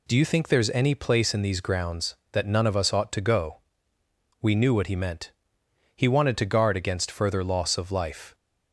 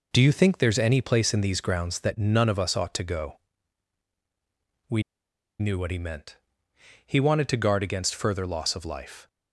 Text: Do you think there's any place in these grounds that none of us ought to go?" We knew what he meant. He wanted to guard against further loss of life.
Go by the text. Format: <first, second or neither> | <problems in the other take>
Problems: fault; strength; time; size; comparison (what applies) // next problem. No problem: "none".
first | pauses between "We" and "knew"; noticeable; at 5.0 s; 0.57 s long